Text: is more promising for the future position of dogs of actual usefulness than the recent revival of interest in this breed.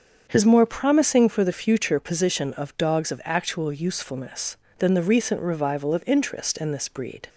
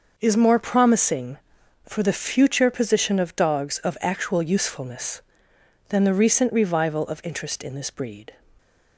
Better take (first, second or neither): second